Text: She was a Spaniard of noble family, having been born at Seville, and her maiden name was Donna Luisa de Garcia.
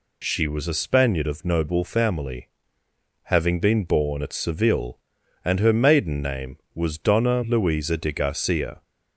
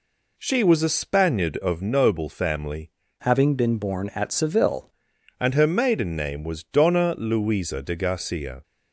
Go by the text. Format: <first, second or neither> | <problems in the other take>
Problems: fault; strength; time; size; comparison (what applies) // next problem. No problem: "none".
first | changes voice from "having" to "Seville"; from 3.1 to 4.8 s; 1.7 s long